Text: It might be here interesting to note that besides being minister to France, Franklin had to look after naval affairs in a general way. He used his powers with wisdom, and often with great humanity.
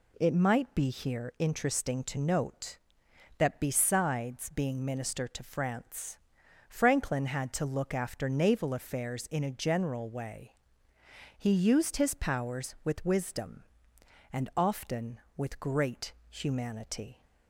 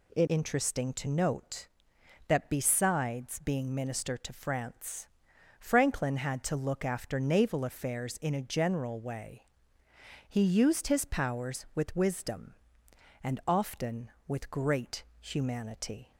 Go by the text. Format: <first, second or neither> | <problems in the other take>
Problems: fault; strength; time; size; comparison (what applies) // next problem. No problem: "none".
first | skips "might be here"; at 0.2 s // pauses between "great" and "humanity"; slight; at 15.0 s; 0.18 s long; slight in the first